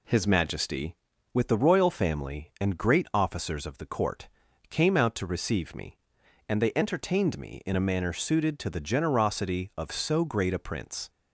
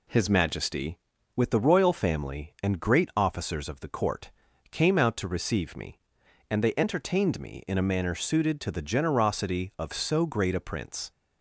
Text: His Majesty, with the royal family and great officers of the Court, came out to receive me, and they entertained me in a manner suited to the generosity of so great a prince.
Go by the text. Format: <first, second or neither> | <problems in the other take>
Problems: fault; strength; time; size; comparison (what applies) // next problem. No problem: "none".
neither | none